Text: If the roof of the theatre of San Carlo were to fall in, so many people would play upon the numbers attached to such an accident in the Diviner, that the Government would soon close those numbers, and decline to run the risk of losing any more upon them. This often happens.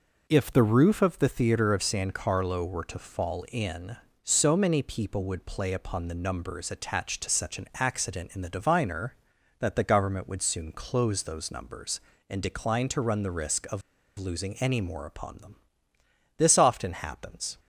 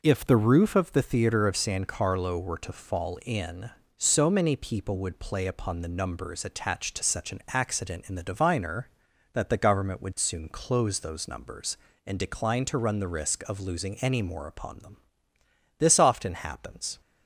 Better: second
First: pauses between "of" and "losing"; at 13.8 s; 0.37 s long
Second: none

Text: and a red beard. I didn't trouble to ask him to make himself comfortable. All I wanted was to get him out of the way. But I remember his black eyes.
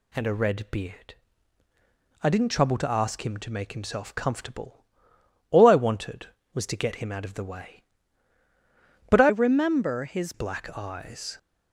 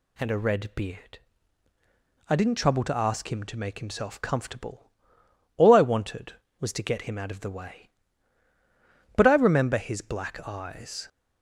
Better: second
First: changes voice from "remember" to "his"; from 9.2 to 10.3 s; 1.1 s long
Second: none

